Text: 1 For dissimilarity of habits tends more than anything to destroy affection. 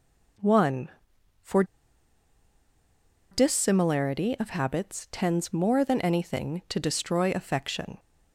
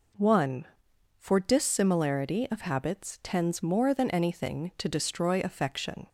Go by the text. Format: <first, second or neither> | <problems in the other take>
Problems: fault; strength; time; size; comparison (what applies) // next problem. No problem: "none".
second | pauses between "For" and "dissimilarity"; strong; at 1.6 s; 1.6 s long